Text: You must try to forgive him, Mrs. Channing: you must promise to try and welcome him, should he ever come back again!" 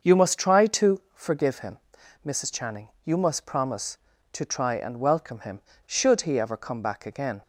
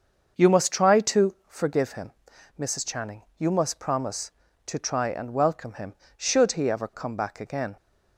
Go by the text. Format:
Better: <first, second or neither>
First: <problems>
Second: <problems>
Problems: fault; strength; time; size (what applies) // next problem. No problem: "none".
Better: neither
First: starts louder than the rest; until 1.1 s; 6.5 dB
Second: starts louder than the rest; until 1.5 s; 6.5 dB